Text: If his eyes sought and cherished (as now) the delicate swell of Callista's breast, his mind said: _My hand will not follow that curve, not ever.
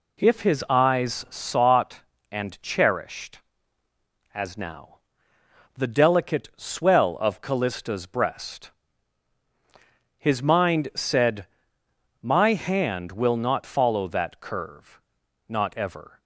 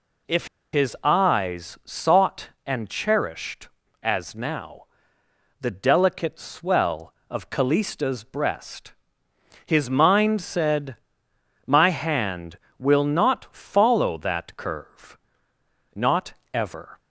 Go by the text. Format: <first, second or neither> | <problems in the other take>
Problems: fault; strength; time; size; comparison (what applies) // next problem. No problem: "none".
first | pauses between "If" and "his"; slight; at 0.4 s; 0.25 s long // pauses between "not" and "ever"; slight; at 16.3 s; 0.20 s long